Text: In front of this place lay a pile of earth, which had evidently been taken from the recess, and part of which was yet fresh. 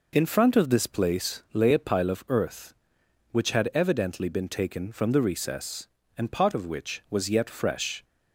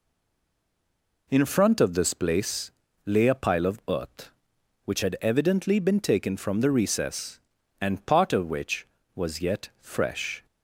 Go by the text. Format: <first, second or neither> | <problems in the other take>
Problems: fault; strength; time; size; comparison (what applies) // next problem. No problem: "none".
first | stays silent before the first word; noticeable; until 1.2 s; 1.2 s long // pauses between "place" and "lay"; slight; at 2.7 s; 0.32 s long